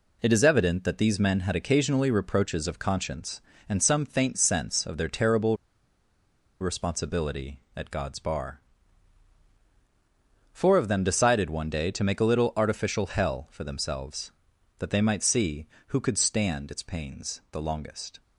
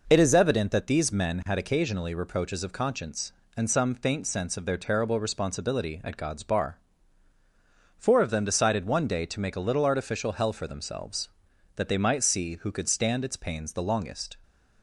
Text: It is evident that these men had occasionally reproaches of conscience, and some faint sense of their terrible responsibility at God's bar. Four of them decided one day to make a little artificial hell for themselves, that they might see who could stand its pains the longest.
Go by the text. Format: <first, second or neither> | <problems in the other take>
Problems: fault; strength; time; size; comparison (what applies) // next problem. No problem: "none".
second | pauses between "terrible" and "responsibility"; at 5.5 s; 1.0 s long